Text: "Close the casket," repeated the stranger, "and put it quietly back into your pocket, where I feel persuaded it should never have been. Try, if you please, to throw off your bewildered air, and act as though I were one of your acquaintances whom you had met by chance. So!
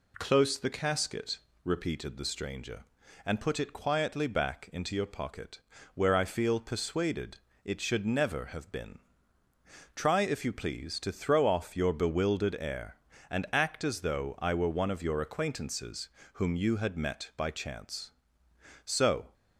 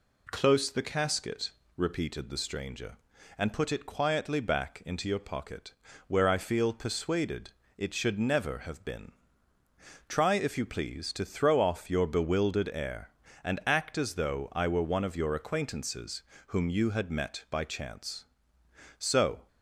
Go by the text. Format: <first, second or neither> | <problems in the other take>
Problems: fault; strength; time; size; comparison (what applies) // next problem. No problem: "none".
neither | pauses between "persuaded" and "it"; slight; the same in both // pauses between "acquaintances" and "whom"; slight; the same in both